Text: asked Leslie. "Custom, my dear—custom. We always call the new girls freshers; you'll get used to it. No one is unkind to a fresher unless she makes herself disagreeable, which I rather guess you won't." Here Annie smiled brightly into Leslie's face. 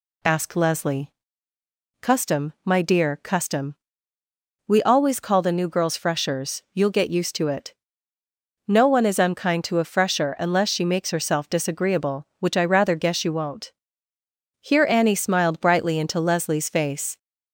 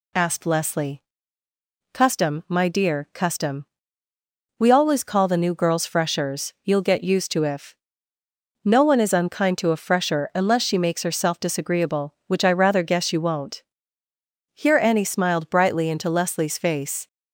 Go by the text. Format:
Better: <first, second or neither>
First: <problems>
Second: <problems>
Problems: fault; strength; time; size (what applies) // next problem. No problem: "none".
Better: first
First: none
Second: says "if" for "it"; at 7.4 s